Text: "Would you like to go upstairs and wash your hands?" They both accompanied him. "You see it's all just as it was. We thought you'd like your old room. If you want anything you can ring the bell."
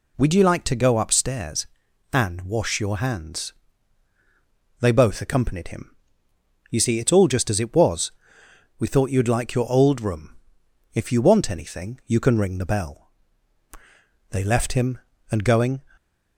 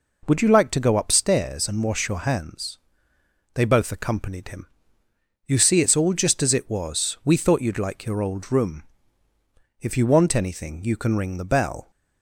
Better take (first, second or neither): second